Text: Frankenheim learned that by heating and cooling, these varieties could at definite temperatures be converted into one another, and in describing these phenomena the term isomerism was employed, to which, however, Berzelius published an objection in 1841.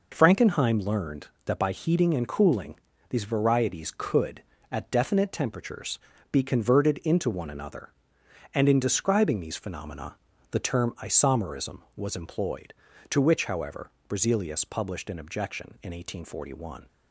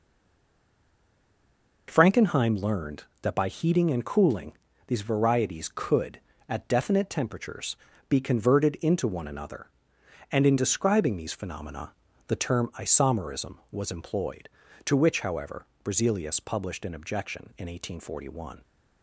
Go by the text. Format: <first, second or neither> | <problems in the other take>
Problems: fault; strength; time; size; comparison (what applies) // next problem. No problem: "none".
first | stays silent before the first word; noticeable; until 1.8 s; 1.8 s long // pauses between "temperatures" and "be"; slight; at 7.7 s; 0.34 s long; slight in the first // pauses between "phenomena" and "the"; slight; at 11.9 s; 0.34 s long; slight in the first